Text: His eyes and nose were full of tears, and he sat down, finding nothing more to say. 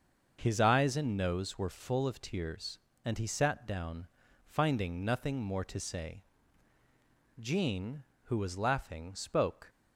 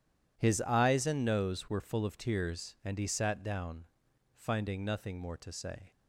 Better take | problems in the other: second | starts louder than the rest; until 1.4 s; 6.5 dB // goes on to say "Jean who was laughing spoke"; strong; from 7.4 s on; 2.2 s long

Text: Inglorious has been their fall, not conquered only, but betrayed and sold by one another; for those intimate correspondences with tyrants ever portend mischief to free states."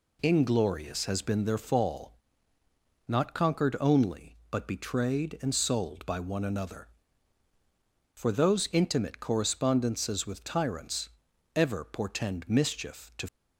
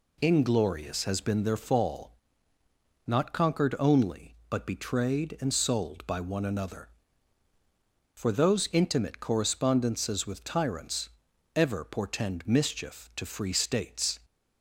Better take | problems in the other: second | pauses between "tyrants" and "ever"; noticeable; at 11.0 s; 0.46 s long; noticeable in the second // stops before "free states"; at 13.2 s

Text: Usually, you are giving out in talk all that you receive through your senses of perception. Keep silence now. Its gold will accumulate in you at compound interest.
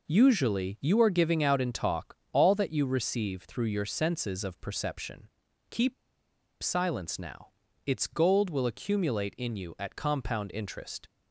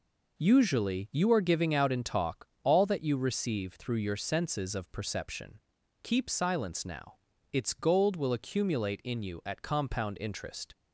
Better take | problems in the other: second | pauses between "talk" and "all"; slight; at 2.1 s; 0.16 s long; slight in the second // pauses between "Keep" and "silence"; noticeable; at 5.9 s; 0.68 s long

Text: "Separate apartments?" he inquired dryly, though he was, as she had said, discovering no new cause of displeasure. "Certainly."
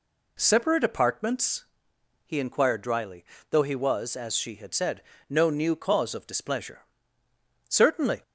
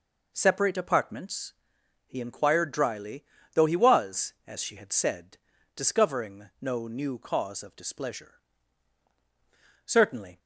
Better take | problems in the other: second | skips "discovering"; at 5.1 s

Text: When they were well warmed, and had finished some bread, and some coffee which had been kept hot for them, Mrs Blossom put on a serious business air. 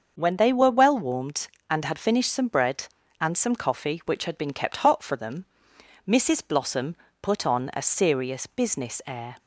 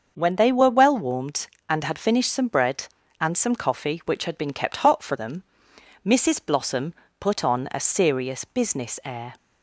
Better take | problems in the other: neither | starts louder than the rest; the same in both // pauses between "Blossom" and "put"; slight; the same in both

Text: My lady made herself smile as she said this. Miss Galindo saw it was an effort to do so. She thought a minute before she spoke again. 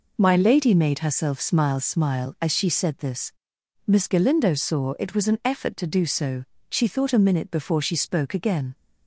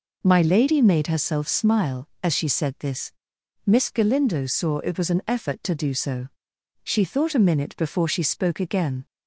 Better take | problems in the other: second | says "smile" twice; at 1.8 s

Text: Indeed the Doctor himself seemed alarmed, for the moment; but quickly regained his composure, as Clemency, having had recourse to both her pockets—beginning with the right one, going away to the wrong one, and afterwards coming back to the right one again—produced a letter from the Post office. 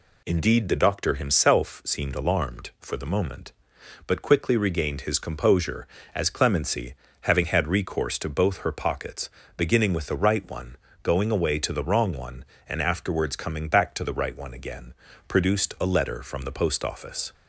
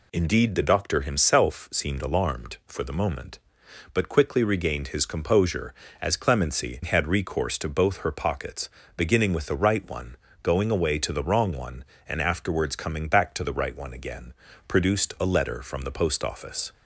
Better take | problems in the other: first | skips "having"; at 6.8 s

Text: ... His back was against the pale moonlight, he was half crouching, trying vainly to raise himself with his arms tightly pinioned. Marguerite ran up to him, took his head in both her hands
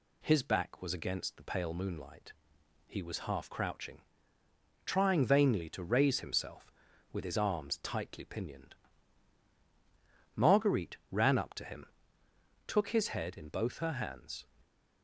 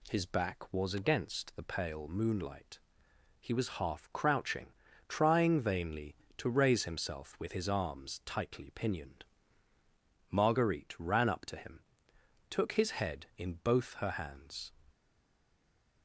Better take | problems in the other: first | stays silent after the last word; from 14.9 s on; 1.1 s long

